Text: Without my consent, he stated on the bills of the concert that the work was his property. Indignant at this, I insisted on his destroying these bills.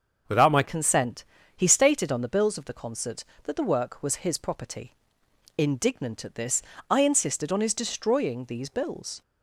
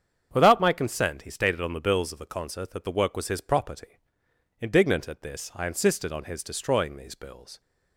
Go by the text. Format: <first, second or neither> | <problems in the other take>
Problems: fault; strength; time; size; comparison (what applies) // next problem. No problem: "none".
second | starts louder than the rest; until 1.6 s; 6.5 dB; strong in the second // changes voice at "consent"; from 0.6 s on; 8.6 s long